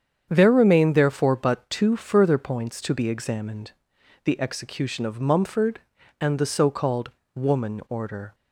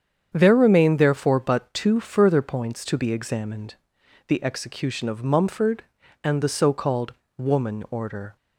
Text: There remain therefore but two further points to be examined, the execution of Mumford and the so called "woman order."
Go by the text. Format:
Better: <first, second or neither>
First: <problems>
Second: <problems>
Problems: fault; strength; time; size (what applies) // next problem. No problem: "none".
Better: neither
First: starts louder than the rest; strong; until 1.3 s; 8 dB // pauses between "called" and "woman"; slight; at 7.1 s; 0.22 s long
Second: starts louder than the rest; strong; until 1.3 s; 8 dB // pauses between "called" and "woman"; slight; at 7.1 s; 0.22 s long